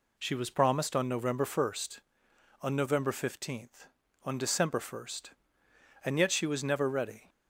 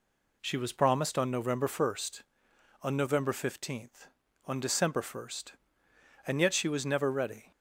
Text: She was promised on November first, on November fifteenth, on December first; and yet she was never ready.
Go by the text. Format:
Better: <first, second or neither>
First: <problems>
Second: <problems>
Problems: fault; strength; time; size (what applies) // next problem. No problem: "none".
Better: neither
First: none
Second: none